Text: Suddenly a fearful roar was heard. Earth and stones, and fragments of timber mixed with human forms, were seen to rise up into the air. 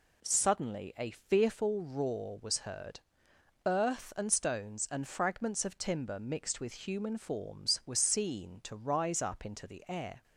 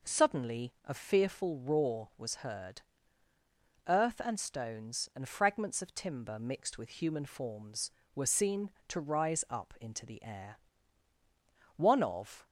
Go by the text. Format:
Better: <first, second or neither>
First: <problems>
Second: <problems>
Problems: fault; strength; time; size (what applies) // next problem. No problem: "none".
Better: first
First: none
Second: goes on to say "One of"; noticeable; from 11.7 s on; 0.68 s long